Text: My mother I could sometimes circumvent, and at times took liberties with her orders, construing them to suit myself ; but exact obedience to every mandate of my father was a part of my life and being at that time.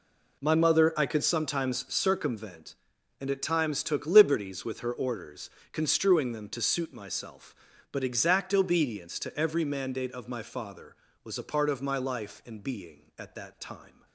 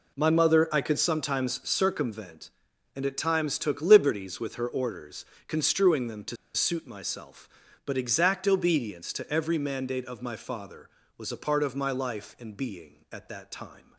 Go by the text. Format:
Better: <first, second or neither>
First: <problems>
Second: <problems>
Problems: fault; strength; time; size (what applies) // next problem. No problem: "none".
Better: first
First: none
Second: pauses between "to" and "suit"; slight; at 6.3 s; 0.19 s long